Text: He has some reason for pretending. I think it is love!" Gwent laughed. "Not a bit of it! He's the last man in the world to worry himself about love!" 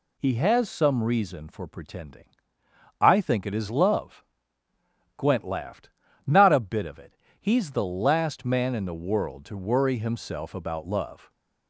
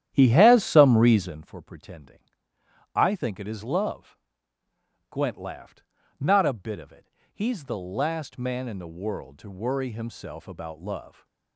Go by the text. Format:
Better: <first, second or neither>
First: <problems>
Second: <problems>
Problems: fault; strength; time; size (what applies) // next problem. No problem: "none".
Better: first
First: none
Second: starts louder than the rest; strong; until 1.5 s; 11 dB